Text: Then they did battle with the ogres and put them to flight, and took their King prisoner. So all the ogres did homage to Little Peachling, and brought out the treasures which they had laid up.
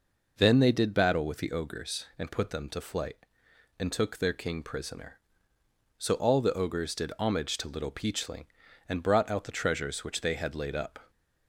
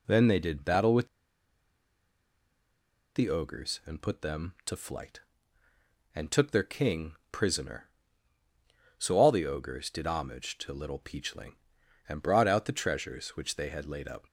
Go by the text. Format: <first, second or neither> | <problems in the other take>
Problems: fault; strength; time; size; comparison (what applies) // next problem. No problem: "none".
first | pauses between "with" and "the"; strong; at 1.0 s; 2.0 s long // pauses between "King" and "prisoner"; slight; at 7.1 s; 0.18 s long